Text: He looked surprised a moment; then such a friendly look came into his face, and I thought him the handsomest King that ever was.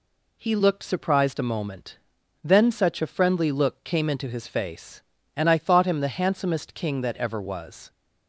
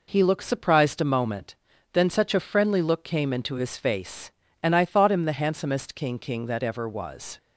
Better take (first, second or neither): first